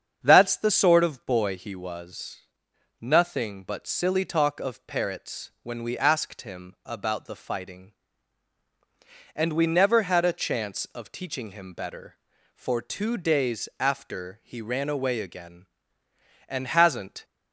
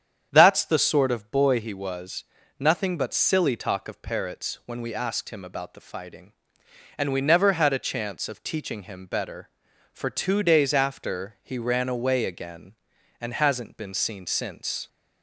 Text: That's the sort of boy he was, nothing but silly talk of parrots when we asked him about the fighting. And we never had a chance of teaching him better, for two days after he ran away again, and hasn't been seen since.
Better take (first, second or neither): second